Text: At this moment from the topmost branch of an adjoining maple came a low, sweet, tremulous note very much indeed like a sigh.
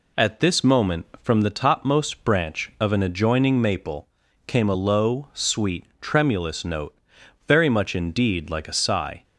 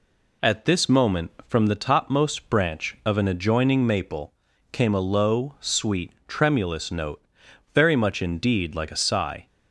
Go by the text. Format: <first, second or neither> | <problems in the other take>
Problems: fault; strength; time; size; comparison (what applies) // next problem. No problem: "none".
neither | pauses between "maple" and "came"; the same in both // pauses between "note" and "very"; noticeable; the same in both